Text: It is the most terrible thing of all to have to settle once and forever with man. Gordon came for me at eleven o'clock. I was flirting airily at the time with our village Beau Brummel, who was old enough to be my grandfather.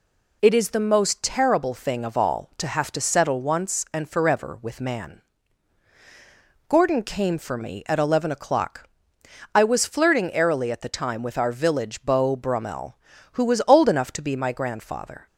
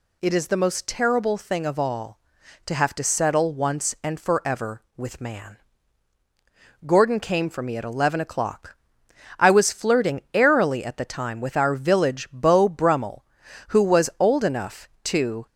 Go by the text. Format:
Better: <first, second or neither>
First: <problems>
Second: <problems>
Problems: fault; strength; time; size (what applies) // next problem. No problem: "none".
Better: first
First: none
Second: stops before "be my grandfather"; at 15.4 s